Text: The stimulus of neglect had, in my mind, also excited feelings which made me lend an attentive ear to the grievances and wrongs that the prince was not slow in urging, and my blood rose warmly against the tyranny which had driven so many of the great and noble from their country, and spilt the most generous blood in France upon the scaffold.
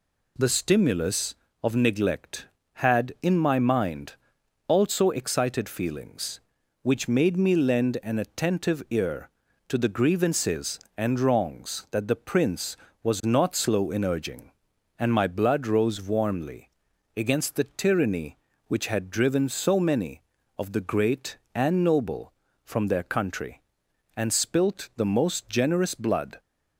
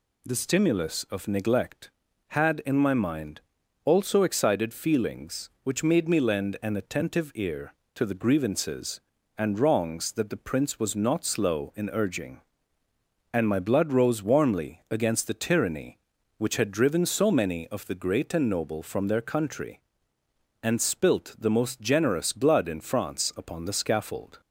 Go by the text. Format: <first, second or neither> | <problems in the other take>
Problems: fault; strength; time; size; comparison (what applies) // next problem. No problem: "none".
second | pauses between "warmly" and "against"; noticeable; at 16.6 s; 0.48 s long // stops before "in France upon the scaffold"; at 26.3 s